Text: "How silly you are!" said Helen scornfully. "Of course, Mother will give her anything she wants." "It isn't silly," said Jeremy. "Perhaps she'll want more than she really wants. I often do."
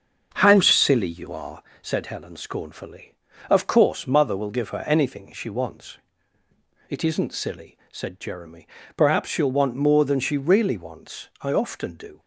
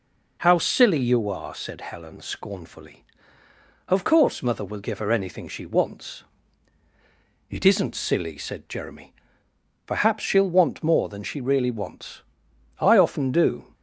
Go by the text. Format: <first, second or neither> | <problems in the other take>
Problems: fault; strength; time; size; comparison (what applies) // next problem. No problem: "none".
second | starts louder than the rest; until 1.8 s; 7 dB